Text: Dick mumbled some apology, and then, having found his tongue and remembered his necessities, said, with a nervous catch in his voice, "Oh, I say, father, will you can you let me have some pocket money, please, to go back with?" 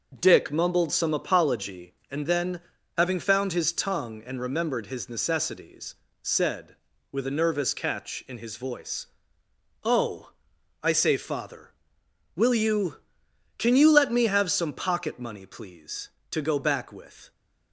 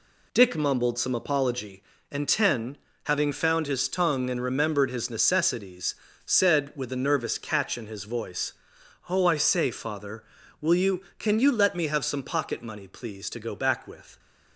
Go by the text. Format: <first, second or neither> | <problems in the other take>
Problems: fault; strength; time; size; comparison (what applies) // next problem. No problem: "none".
first | says "ten" for "then"; at 2.2 s